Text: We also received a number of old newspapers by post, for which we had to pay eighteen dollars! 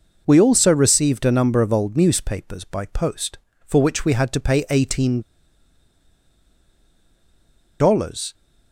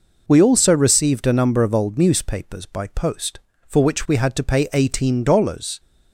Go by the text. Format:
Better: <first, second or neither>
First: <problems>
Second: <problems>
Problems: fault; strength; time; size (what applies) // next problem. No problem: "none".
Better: second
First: pauses between "eighteen" and "dollars"; strong; at 5.2 s; 2.5 s long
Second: none